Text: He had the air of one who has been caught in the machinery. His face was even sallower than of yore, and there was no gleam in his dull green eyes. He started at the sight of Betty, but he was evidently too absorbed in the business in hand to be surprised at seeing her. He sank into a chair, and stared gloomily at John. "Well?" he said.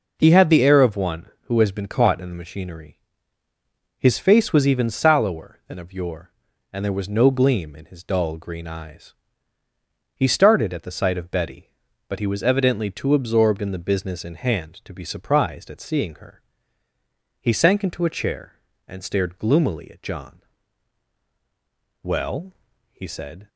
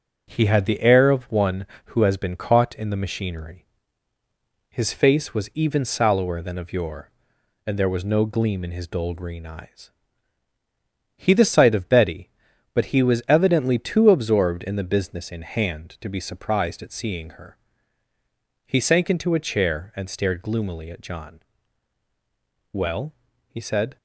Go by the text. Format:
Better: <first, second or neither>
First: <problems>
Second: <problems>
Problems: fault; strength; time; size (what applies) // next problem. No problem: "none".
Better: first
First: none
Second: starts louder than the rest; until 1.2 s; 6.5 dB // skips "started at"; at 11.3 s